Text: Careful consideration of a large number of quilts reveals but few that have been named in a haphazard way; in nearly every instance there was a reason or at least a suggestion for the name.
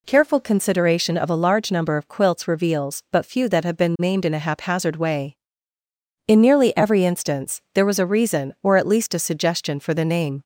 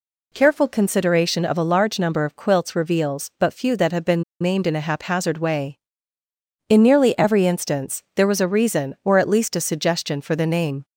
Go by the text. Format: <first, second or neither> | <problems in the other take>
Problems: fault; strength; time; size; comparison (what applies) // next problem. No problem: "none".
first | pauses between "been" and "named"; slight; at 4.2 s; 0.17 s long